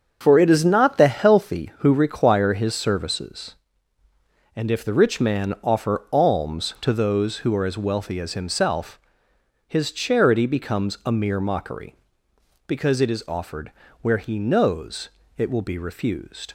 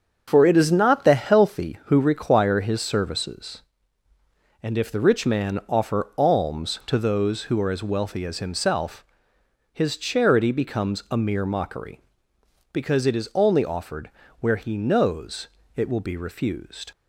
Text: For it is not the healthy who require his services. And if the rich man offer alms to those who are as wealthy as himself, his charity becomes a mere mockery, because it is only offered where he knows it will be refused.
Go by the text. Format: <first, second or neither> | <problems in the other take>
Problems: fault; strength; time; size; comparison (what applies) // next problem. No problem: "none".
second | starts louder than the rest; strong; until 1.2 s; 7 dB; strong in the second // skips "only"; at 13.2 s // pauses between "offered" and "where"; slight; at 13.7 s; 0.32 s long; slight in the second // pauses between "knows" and "it"; slight; at 15.0 s; 0.30 s long; slight in the second